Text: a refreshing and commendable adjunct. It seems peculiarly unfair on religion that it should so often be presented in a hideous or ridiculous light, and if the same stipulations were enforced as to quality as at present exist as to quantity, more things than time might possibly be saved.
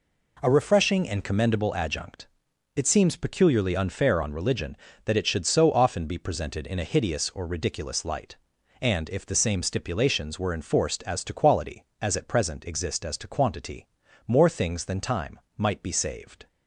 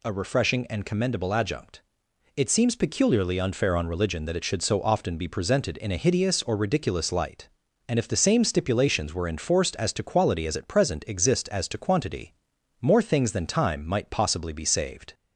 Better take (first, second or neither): second